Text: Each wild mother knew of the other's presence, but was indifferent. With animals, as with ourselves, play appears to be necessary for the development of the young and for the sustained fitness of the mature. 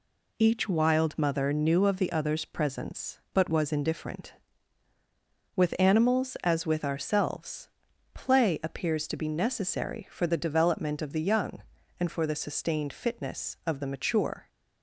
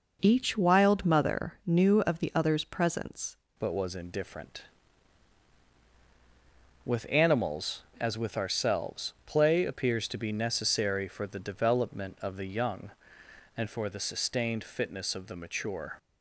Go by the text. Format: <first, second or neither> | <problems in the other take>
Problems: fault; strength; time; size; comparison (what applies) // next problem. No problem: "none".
first | changes voice at "but"; from 3.5 s on; 12.4 s long